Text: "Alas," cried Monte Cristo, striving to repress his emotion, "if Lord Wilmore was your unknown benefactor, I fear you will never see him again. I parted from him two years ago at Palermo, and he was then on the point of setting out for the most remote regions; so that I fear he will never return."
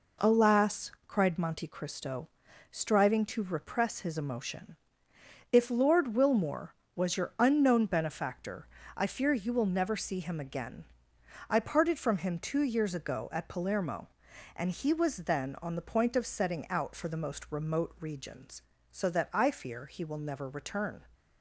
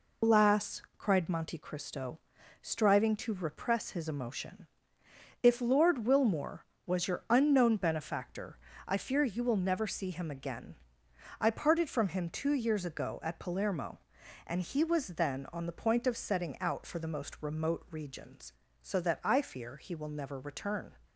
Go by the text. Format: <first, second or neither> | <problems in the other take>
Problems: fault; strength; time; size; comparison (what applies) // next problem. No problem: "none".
first | loses the start of "Alas"; at 0.2 s; 135 ms